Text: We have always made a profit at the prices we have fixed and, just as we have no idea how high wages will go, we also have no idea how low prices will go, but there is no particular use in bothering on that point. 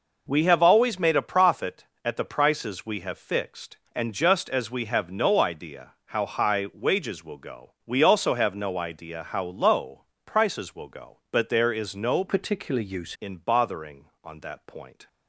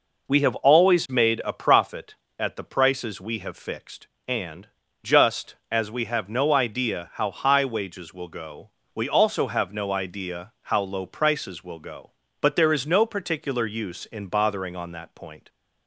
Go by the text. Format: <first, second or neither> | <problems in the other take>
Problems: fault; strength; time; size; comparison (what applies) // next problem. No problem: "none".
second | pauses between "low" and "prices"; slight; at 10.0 s; 0.22 s long // changes voice from "particular" to "use"; from 12.2 to 13.1 s; 0.9 s long